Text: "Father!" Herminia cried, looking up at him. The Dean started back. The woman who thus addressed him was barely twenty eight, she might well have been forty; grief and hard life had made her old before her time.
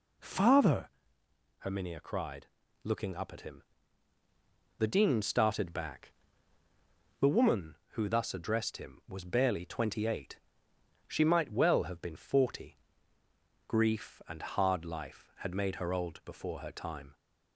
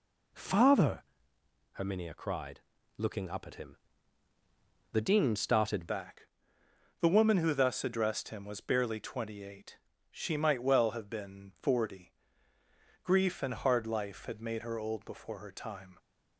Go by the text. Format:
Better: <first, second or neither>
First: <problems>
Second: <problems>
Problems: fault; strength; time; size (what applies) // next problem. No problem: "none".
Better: first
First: none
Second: changes voice at "back"; from 5.8 s on; 10.1 s long